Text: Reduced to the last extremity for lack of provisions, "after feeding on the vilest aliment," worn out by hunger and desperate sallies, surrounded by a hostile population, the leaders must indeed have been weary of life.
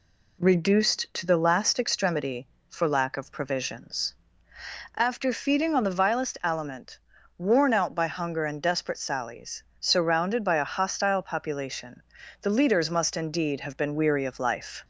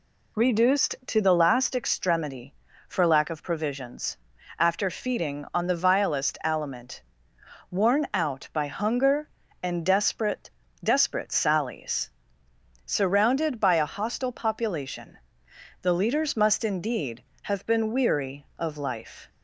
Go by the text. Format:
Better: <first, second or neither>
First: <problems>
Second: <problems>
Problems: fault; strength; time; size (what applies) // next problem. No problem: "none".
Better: first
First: none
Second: says "desperate" twice; at 10.8 s